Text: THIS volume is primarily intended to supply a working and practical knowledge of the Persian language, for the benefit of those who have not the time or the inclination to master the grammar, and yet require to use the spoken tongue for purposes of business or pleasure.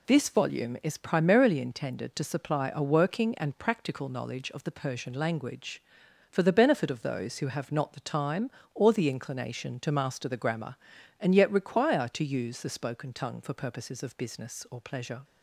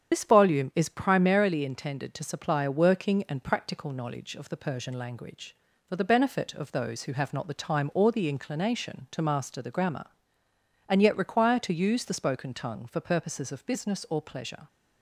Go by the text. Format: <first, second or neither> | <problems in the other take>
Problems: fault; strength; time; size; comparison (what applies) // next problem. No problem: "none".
first | loses the start of "THIS"; at 0.1 s; 50 ms // starts louder than the rest; strong; until 1.1 s; 8.5 dB